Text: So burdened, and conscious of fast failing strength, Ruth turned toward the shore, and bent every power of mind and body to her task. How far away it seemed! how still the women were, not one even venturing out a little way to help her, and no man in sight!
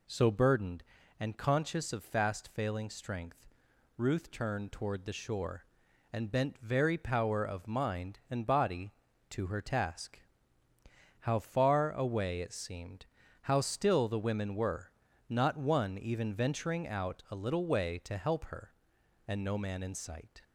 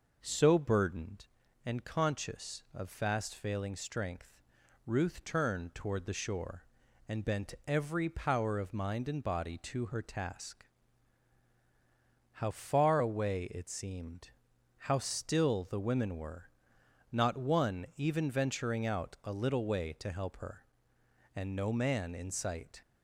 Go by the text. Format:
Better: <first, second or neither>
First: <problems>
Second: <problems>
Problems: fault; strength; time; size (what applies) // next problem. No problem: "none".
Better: second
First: says "very" for "every"; at 6.5 s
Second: none